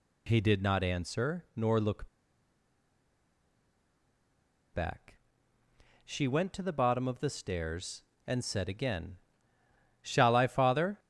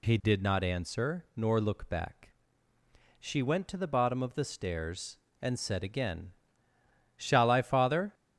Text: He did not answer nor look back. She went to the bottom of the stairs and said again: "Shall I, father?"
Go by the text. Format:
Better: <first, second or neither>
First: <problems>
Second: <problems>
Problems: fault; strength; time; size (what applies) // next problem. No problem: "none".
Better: second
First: pauses between "look" and "back"; strong; at 2.0 s; 2.6 s long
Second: none